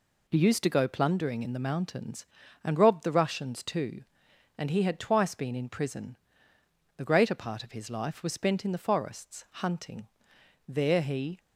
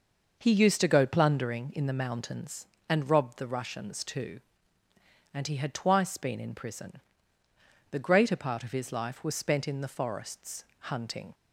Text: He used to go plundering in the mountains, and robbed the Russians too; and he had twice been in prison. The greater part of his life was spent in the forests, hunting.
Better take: second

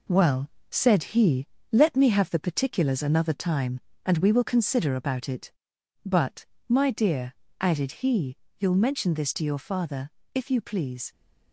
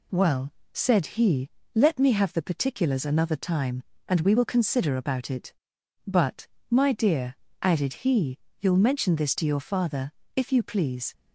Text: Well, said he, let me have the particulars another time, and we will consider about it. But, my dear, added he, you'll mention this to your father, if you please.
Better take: second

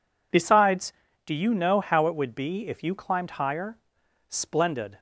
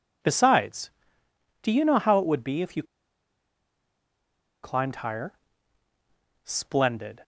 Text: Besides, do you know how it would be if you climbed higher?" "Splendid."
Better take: first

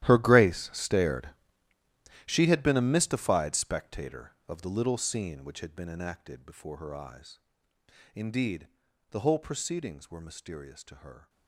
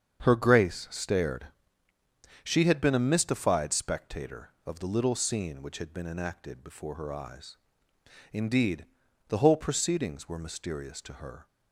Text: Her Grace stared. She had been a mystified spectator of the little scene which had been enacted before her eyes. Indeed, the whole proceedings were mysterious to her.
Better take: second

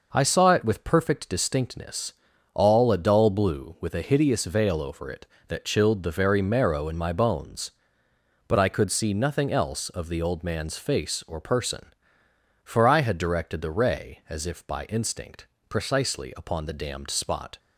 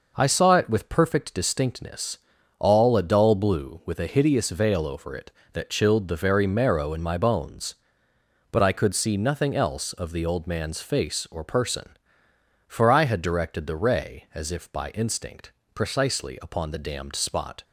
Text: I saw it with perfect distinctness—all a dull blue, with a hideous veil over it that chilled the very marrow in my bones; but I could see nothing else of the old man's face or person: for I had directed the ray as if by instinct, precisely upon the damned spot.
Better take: neither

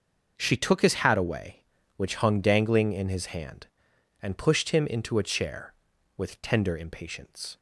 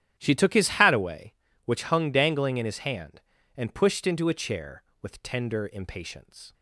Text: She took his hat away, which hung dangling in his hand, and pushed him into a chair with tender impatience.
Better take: first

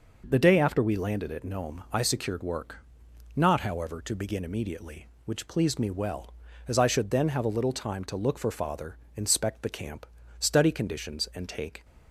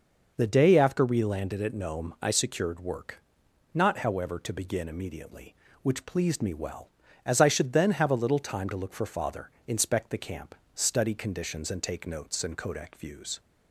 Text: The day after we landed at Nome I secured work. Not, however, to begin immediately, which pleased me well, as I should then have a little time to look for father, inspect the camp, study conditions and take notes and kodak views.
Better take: second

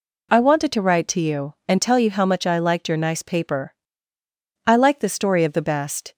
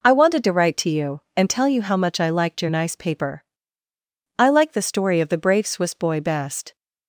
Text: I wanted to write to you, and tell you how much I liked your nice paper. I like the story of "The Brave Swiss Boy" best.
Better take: second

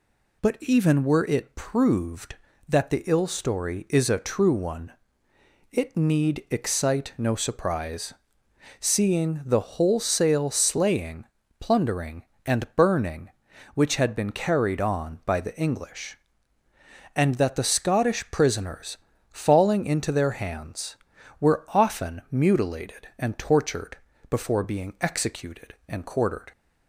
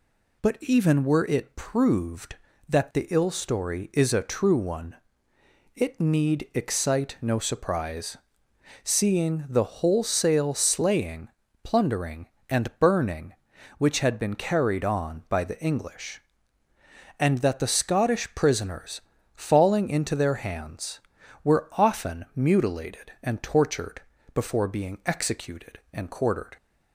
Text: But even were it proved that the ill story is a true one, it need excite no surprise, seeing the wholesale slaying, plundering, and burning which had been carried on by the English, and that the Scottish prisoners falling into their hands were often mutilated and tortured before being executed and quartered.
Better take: neither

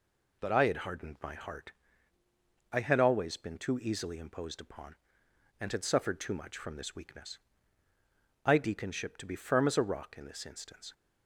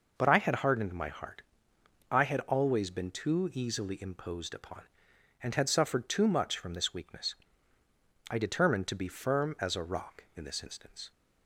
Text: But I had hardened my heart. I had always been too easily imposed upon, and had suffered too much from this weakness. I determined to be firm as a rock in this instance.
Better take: second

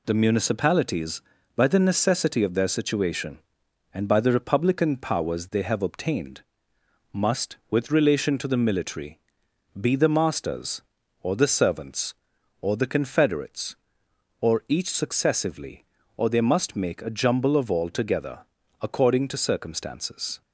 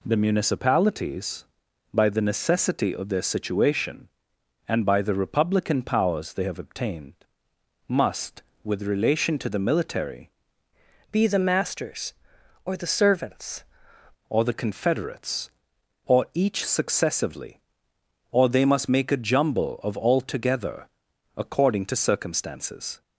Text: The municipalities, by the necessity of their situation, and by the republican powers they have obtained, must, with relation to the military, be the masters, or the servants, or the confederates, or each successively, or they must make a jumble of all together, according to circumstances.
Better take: first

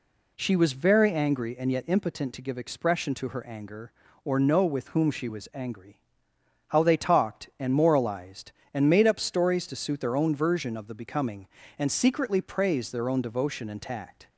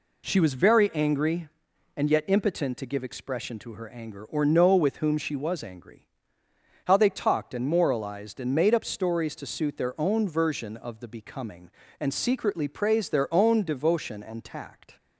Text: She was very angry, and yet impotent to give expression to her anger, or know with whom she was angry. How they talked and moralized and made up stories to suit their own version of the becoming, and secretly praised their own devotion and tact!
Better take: neither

